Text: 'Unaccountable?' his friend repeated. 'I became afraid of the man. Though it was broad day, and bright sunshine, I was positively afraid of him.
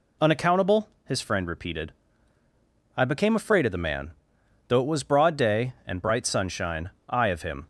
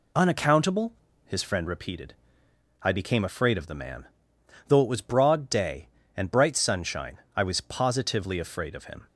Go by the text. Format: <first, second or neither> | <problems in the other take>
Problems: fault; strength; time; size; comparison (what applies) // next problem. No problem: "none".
second | skips "was positively afraid"; at 7.2 s